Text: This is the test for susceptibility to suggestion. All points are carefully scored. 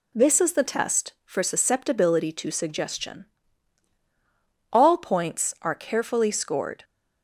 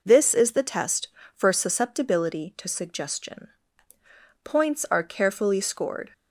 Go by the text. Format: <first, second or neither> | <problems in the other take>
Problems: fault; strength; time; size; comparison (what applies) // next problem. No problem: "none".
first | skips "All"; at 3.9 s